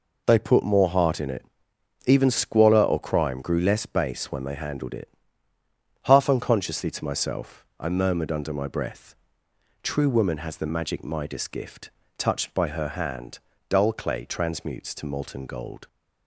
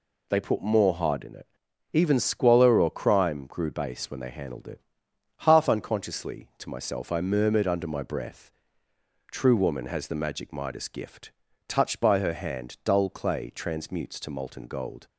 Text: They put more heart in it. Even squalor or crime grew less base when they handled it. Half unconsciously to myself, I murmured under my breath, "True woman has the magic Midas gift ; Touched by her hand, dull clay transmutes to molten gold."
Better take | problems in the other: first | skips "less"; at 3.7 s

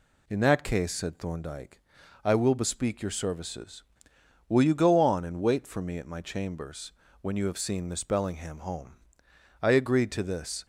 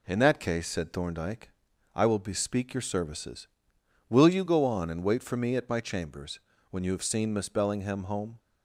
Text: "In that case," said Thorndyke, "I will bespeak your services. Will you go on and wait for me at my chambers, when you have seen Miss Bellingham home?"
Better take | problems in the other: second | goes on to say "I agreed to this"; noticeable; from 9.6 s on; 1.0 s long

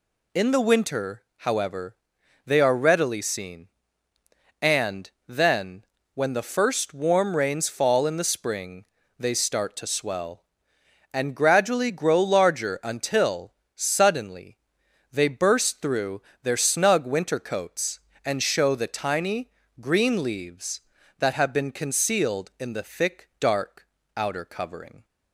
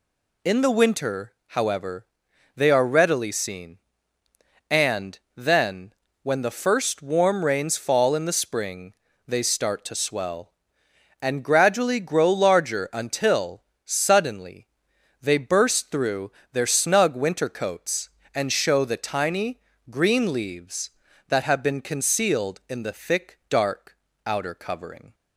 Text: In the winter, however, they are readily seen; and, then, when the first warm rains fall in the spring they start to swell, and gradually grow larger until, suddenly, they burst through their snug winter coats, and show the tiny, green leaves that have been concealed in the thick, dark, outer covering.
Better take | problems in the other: neither | pauses between "spring" and "they"; slight; the same in both // pauses between "through" and "their"; slight; the same in both

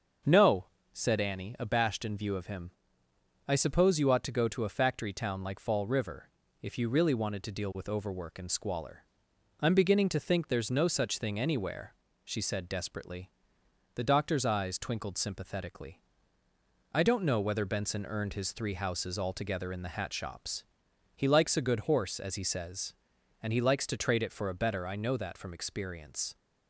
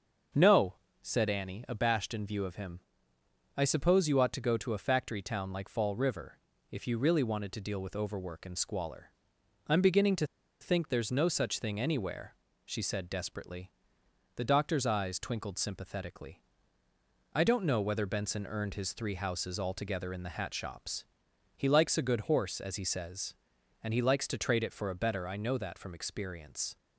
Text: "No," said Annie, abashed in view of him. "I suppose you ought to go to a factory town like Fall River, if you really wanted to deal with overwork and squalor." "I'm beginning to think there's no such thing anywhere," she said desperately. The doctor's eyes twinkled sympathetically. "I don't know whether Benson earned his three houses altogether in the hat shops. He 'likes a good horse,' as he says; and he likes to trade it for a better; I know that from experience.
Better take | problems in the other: first | starts louder than the rest; until 1.5 s; 6.5 dB; also in the first // pauses between "to" and "think"; slight; at 10.2 s; 0.34 s long

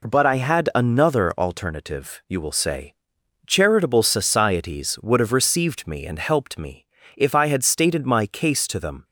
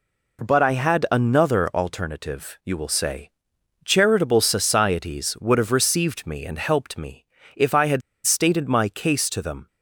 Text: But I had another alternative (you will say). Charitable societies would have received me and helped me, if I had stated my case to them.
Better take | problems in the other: first | pauses between "had" and "stated"; slight; at 8.0 s; 0.23 s long

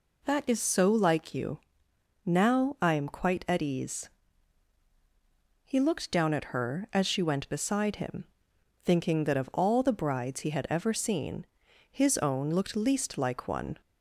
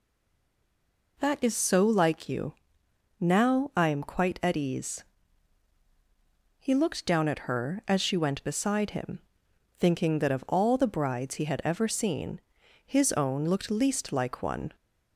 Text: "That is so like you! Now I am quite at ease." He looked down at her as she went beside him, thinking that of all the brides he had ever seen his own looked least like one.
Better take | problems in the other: first | stays silent before the first word; noticeable; until 1.1 s; 1.1 s long // pauses between "seen" and "his"; noticeable; at 12.3 s; 0.46 s long; noticeable in the first

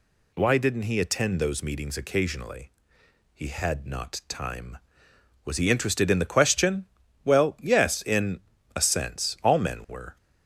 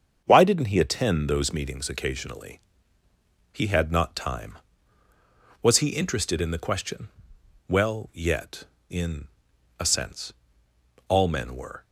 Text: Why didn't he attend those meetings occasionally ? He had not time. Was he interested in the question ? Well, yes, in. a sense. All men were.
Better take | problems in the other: first | starts louder than the rest; until 1.2 s; 7 dB // says "yet" for "yes"; at 8.1 s

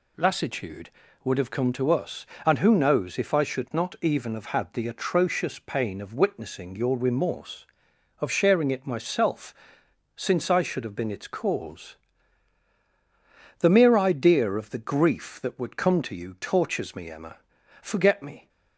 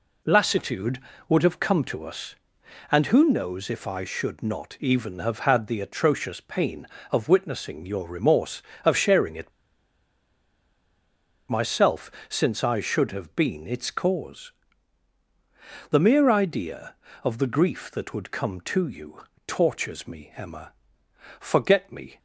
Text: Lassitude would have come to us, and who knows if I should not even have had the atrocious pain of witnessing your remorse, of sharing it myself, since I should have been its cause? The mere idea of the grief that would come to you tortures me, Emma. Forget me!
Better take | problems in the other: first | pauses between "it" and "myself"; strong; at 9.5 s; 1.9 s long // pauses between "you" and "tortures"; slight; at 19.2 s; 0.24 s long

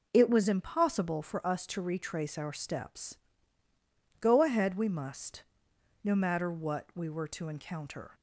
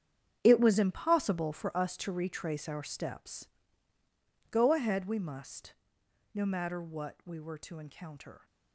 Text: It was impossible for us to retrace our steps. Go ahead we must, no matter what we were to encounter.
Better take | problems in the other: first | gets quieter; strong; throughout; 12.5 dB

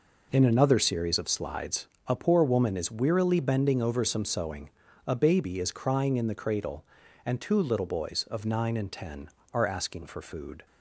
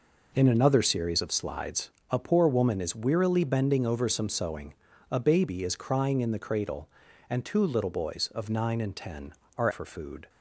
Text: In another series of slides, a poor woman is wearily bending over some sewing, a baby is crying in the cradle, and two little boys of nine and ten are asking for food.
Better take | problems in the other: first | skips "asking"; at 9.6 s

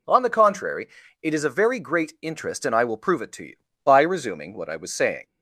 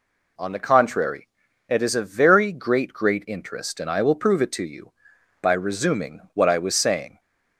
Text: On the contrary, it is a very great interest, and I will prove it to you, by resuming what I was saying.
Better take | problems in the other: first | says "great" twice; at 2.9 s

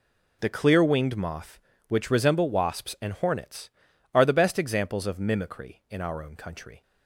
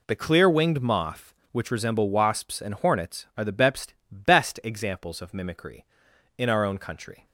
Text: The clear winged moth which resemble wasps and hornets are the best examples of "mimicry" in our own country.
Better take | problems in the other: first | says "best" twice; at 4.1 s

